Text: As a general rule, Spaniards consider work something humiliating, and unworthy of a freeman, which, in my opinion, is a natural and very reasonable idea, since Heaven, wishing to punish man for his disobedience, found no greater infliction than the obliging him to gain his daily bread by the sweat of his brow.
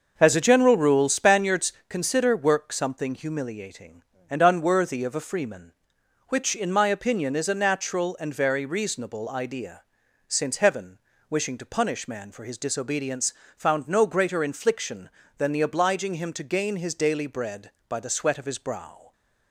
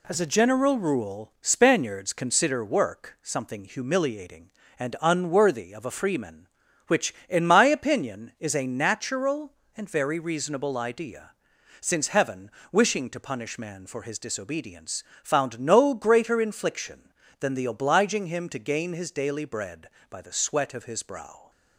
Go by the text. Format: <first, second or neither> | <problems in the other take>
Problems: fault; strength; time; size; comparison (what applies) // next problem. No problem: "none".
second | starts louder than the rest; noticeable; until 1.9 s; 6 dB // pauses between "Spaniards" and "consider"; slight; at 1.7 s; 0.16 s long